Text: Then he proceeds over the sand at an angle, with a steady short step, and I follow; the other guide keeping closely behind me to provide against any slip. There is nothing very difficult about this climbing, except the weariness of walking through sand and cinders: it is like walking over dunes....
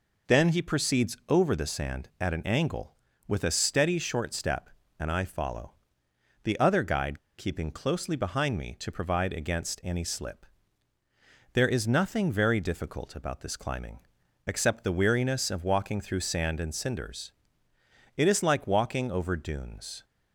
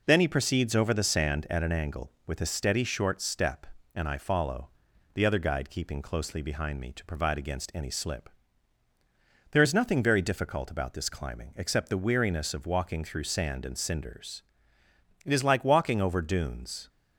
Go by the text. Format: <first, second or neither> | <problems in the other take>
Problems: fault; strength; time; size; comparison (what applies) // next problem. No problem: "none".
second | pauses between "guide" and "keeping"; slight; at 7.1 s; 0.18 s long